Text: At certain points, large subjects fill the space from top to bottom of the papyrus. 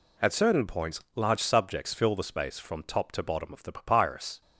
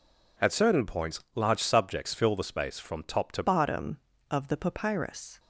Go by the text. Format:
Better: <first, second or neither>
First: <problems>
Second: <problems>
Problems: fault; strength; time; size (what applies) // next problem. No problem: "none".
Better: first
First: none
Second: changes voice at "bottom"; from 3.4 s on; 1.9 s long